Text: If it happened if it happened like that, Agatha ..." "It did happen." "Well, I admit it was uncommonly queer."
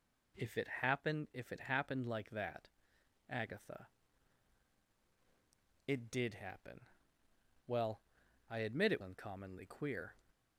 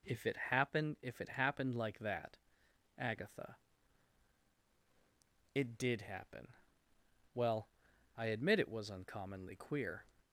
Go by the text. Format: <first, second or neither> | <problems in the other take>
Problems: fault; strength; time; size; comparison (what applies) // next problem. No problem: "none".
second | skips "was"; at 9.0 s